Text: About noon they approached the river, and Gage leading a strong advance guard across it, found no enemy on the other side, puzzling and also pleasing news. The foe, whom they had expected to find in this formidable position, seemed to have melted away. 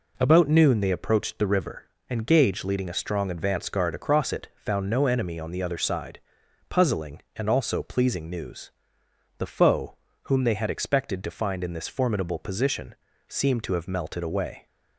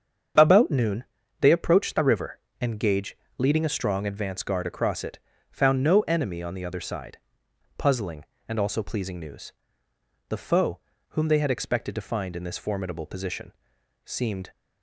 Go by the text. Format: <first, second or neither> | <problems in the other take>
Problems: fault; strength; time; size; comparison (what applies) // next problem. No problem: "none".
first | starts louder than the rest; strong; until 1.7 s; 7 dB // pauses between "noon" and "they"; slight; at 1.0 s; 0.36 s long // pauses between "Gage" and "leading"; slight; at 3.1 s; 0.22 s long // stops before "to have melted away"; at 14.5 s